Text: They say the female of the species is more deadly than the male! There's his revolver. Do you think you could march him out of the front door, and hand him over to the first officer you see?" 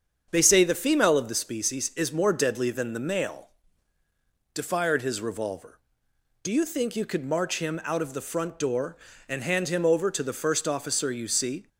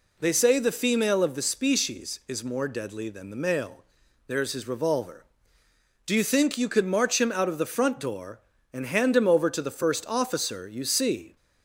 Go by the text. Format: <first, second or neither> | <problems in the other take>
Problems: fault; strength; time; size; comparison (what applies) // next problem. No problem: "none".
second | starts louder than the rest; strong; until 1.3 s; 7.5 dB // says "Defired" for "There's"; at 4.5 s